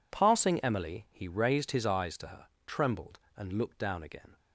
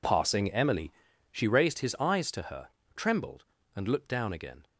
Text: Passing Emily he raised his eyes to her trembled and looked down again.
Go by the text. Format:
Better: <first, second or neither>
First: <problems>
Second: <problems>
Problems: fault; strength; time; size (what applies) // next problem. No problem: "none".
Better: first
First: pauses between "her" and "trembled"; slight; at 2.4 s; 0.18 s long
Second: says "she" for "he"; at 1.3 s // pauses between "her" and "trembled"; slight; at 2.6 s; 0.26 s long